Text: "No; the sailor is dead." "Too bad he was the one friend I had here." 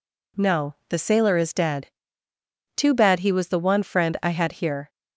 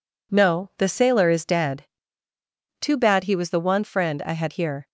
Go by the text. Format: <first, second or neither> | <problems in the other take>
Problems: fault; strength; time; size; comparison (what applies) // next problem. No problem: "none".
neither | none